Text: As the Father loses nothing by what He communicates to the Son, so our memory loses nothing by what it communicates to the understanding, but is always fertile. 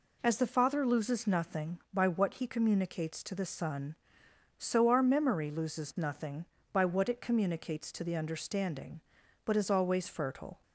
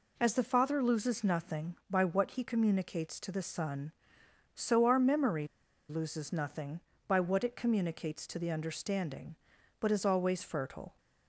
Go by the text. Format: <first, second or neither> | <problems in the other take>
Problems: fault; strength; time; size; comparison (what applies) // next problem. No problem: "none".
first | pauses between "memory" and "loses"; at 5.4 s; 0.43 s long